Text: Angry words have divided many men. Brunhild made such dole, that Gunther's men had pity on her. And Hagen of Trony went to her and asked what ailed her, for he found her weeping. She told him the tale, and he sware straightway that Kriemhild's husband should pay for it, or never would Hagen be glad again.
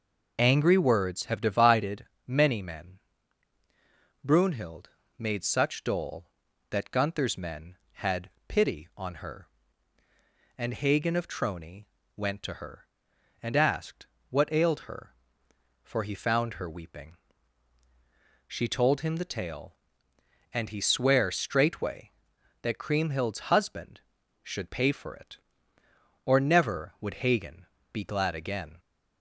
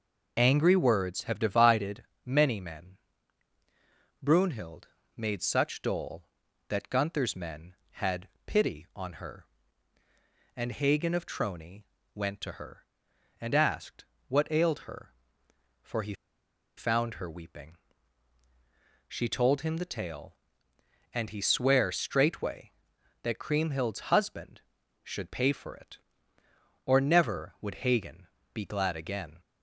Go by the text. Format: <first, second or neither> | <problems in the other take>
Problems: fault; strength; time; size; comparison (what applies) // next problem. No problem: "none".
first | pauses between "divided" and "many"; slight; at 2.0 s; 0.20 s long; slight in the first // pauses between "Brunhild" and "made"; slight; at 4.8 s; 0.28 s long; slight in the first // pauses between "had" and "pity"; slight; at 8.2 s; 0.18 s long; slight in the first // pauses between "Trony" and "went"; slight; at 11.8 s; 0.32 s long; slight in the first // pauses between "asked" and "what"; slight; at 14.0 s; 0.22 s long; slight in the first // pauses between "he" and "found"; noticeable; at 16.1 s; 0.62 s long // pauses between "Hagen" and "be"; slight; at 28.2 s; 0.24 s long; slight in the first